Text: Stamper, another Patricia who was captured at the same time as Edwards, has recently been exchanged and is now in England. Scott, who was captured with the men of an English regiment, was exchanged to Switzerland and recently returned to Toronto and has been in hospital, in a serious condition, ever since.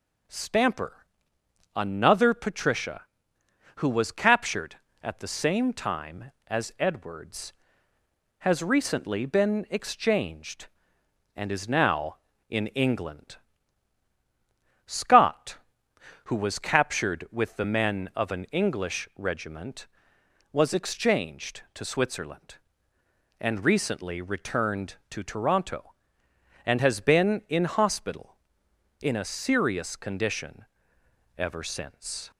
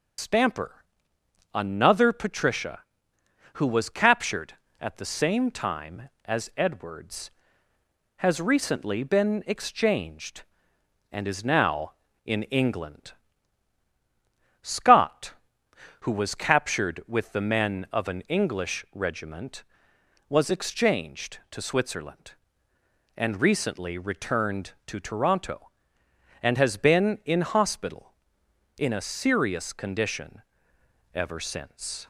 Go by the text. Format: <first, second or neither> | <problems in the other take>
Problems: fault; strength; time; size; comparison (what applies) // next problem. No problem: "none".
first | loses the start of "Stamper"; at 0.1 s; 125 ms